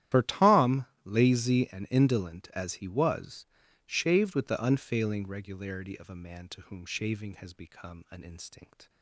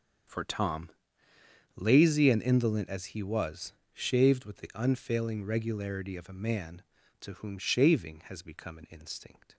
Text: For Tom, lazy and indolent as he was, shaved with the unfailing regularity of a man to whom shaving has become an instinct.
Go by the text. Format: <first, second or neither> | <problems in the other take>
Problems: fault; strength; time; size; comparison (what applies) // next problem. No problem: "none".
second | loses the start of "For"; at 0.1 s; 85 ms // starts louder than the rest; strong; until 1.2 s; 12 dB; also in the second